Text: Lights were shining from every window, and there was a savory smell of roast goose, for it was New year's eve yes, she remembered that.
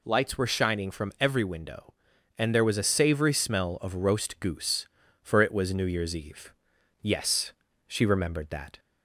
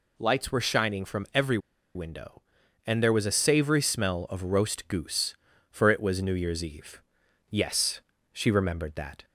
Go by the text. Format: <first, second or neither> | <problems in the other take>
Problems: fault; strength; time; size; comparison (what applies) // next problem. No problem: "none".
first | pauses between "every" and "window"; at 1.5 s; 0.37 s long // pauses between "eve" and "yes"; noticeable; at 7.0 s; 0.48 s long; noticeable in the first